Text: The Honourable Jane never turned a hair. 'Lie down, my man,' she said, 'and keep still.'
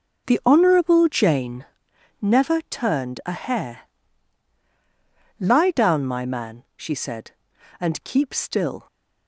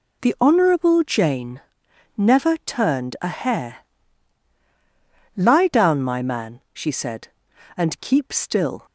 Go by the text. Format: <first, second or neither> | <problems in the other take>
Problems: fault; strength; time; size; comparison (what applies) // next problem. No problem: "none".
second | starts louder than the rest; noticeable; until 1.9 s; 6 dB // pauses between "Jane" and "never"; noticeable; at 1.6 s; 0.56 s long; noticeable in the second